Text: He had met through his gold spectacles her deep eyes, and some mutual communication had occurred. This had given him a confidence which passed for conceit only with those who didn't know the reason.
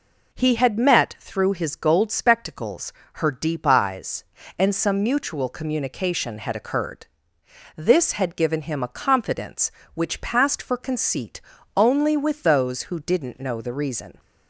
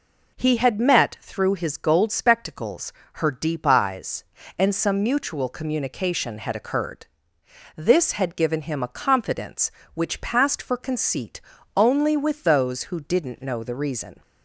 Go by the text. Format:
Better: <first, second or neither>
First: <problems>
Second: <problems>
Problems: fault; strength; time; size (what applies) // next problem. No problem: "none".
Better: neither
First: pauses between "spectacles" and "her"; slight; at 2.9 s; 0.22 s long // pauses between "conceit" and "only"; slight; at 11.3 s; 0.36 s long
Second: pauses between "spectacles" and "her"; slight; at 2.9 s; 0.22 s long // pauses between "conceit" and "only"; slight; at 11.3 s; 0.36 s long